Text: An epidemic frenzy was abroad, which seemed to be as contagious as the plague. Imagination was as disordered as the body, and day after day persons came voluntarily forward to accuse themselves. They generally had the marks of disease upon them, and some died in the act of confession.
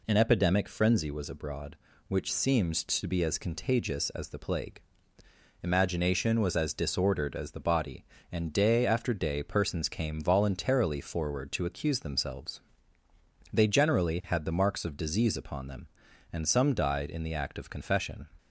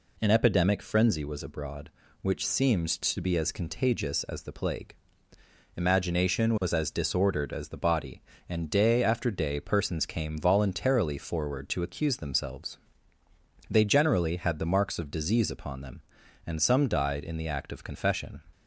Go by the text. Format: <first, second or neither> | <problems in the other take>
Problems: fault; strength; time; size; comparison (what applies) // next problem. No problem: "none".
neither | none